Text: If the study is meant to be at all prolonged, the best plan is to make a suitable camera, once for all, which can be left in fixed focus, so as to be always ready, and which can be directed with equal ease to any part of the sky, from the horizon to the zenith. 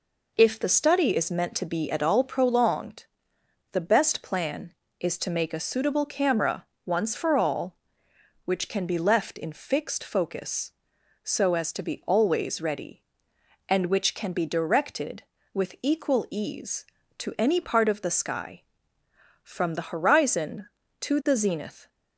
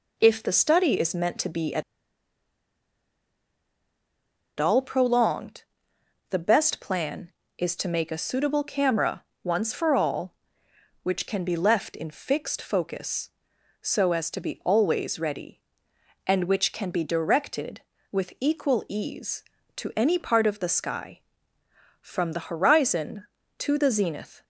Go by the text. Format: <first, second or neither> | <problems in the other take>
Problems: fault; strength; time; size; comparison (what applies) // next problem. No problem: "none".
first | pauses between "at" and "all"; strong; at 1.8 s; 2.7 s long